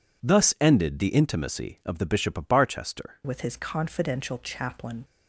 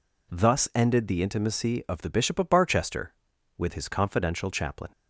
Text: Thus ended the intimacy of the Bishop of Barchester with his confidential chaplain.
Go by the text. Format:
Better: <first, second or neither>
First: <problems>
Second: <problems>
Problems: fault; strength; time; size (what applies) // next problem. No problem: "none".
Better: second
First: changes voice at "with"; from 3.2 s on; 1.8 s long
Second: none